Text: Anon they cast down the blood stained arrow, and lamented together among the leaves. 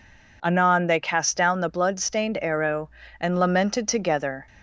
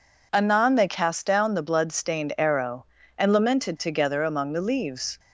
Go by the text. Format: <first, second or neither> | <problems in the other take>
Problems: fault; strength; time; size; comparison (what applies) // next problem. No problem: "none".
second | stops before "among the leaves"; at 4.4 s